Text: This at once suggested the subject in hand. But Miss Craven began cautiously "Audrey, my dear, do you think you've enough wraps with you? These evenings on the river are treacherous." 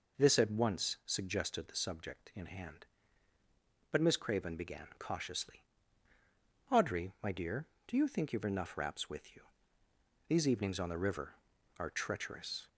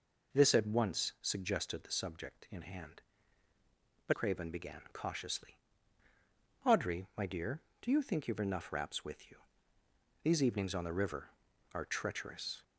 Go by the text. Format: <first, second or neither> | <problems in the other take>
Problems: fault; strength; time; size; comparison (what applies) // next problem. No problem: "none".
first | skips "Miss"; at 4.1 s // pauses between "cautiously" and "Audrey"; at 5.5 s; 1.0 s long; also in the first